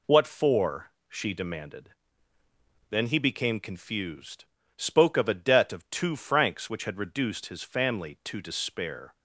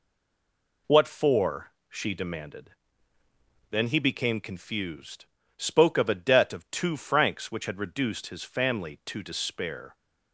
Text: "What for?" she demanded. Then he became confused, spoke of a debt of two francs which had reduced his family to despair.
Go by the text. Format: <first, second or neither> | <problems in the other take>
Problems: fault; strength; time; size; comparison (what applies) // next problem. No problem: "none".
first | stays silent before the first word; slight; until 0.8 s; 0.8 s long